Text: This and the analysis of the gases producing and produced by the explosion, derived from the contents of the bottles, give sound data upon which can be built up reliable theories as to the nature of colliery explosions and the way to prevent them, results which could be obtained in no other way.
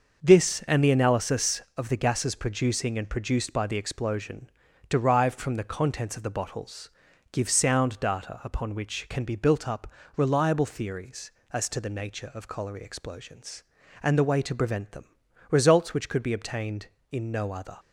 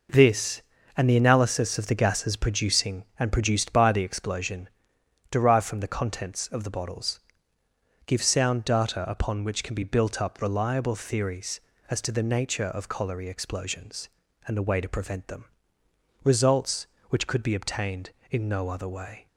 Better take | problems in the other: second | starts louder than the rest; until 1.2 s; 6 dB // pauses between "up" and "reliable"; slight; at 9.8 s; 0.30 s long // stops before "way"; at 17.7 s

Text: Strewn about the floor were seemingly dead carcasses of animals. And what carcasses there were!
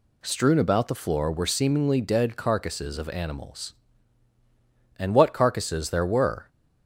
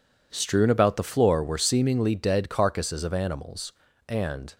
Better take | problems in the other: first | stops before "what carcasses there were"; at 4.5 s

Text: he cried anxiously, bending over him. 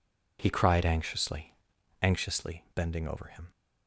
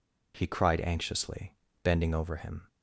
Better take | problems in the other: second | says "anxiously" twice; at 2.0 s

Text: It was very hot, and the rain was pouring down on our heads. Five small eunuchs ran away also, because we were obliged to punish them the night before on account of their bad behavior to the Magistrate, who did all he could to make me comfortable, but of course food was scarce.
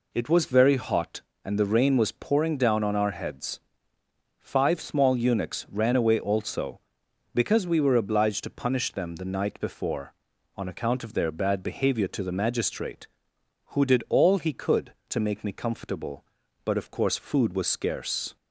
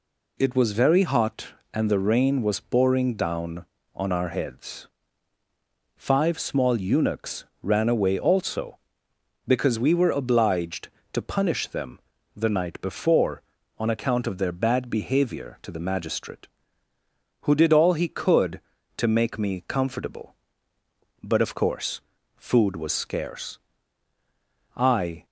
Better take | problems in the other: first | pauses between "eunuchs" and "ran"; slight; at 7.4 s; 0.18 s long // pauses between "them" and "the"; slight; at 11.9 s; 0.36 s long // pauses between "course" and "food"; slight; at 22.0 s; 0.36 s long // goes on to say "I"; from 24.7 s on; 0.50 s long

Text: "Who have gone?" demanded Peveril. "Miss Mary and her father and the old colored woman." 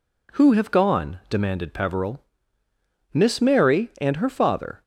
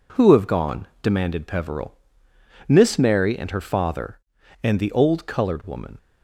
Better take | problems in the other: second | stops before "and the old colored woman"; at 4.8 s

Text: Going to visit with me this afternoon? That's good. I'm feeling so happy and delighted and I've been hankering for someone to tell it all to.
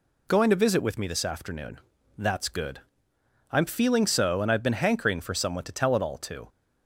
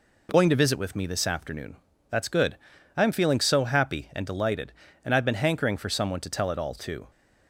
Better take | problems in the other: second | skips "happy and delighted"; at 4.4 s

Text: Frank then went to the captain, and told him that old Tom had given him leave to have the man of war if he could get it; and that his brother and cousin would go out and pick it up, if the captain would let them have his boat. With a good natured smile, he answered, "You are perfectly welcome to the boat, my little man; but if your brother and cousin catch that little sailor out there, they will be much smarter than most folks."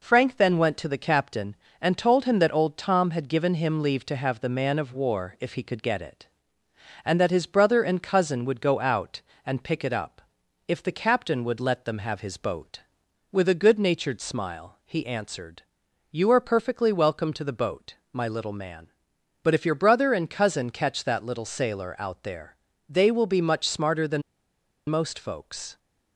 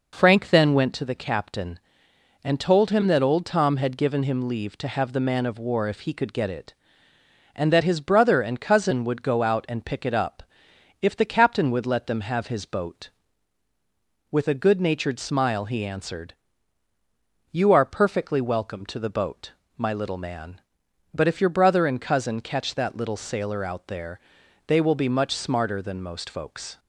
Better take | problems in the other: second | pauses between "than" and "most"; noticeable; at 24.2 s; 0.68 s long

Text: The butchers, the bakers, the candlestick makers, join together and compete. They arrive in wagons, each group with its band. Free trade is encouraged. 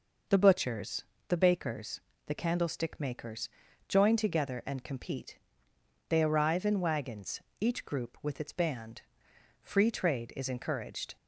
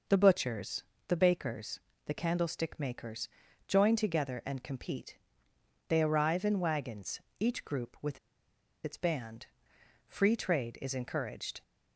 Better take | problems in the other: first | pauses between "with" and "its"; noticeable; at 8.1 s; 0.67 s long

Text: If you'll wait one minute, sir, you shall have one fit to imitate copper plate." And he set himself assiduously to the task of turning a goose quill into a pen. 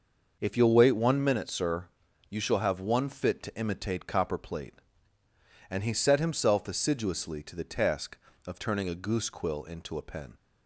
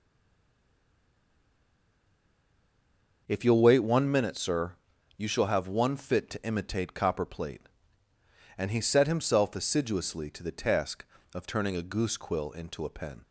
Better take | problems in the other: first | stays silent before the first word; strong; until 3.2 s; 3.2 s long

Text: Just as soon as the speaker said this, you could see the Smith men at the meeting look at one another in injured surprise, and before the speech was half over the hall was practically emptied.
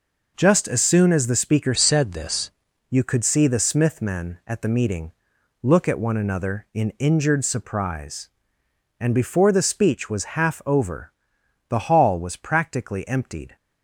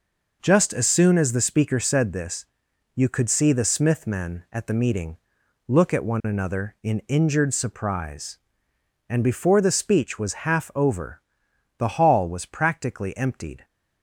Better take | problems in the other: second | changes voice from "said" to "this"; from 1.7 to 2.5 s; 0.8 s long // pauses between "meeting" and "look"; noticeable; at 5.1 s; 0.50 s long; noticeable in the second // pauses between "over" and "the"; noticeable; at 11.1 s; 0.56 s long; noticeable in the second

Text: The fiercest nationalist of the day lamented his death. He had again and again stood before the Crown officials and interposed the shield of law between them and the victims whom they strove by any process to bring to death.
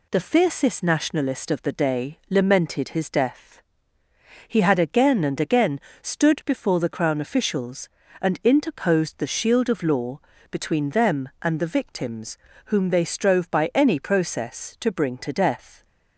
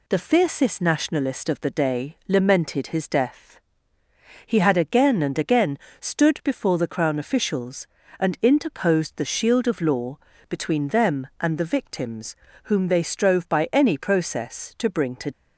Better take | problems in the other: first | pauses between "again" and "stood"; slight; at 5.7 s; 0.20 s long; slight in the first // pauses between "law" and "between"; slight; at 10.1 s; 0.30 s long; slight in the first // pauses between "victims" and "whom"; slight; at 12.3 s; 0.30 s long; slight in the first // stops before "death"; at 15.3 s

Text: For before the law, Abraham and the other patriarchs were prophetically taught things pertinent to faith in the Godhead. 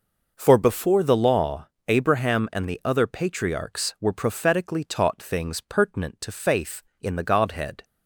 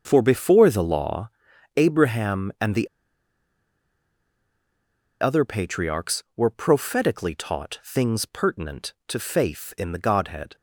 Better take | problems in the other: first | starts louder than the rest; until 1.0 s; 6.5 dB // pauses between "the" and "other"; strong; at 2.8 s; 2.3 s long

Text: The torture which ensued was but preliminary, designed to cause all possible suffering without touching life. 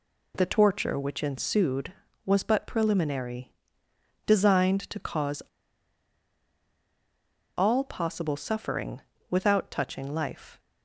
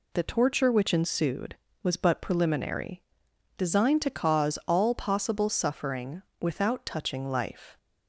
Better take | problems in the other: second | pauses between "cause" and "all"; strong; at 5.4 s; 2.1 s long // pauses between "suffering" and "without"; slight; at 8.9 s; 0.30 s long; slight in the second

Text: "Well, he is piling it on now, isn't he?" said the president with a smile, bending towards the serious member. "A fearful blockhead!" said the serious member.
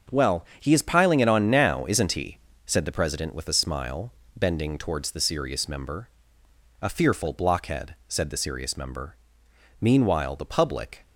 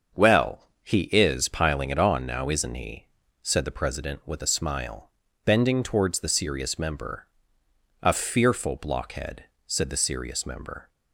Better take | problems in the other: second | starts louder than the rest; until 1.2 s; 6.5 dB; also in the second // goes on to say "Meanwhile the public"; noticeable; from 9.8 s on; 1.2 s long

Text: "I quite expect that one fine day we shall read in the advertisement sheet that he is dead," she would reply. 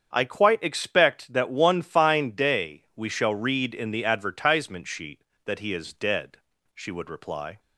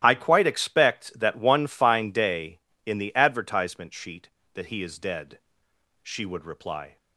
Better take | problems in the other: first | starts louder than the rest; strong; until 1.0 s; 12.5 dB; strong in the first // skips "we shall read"; at 2.7 s

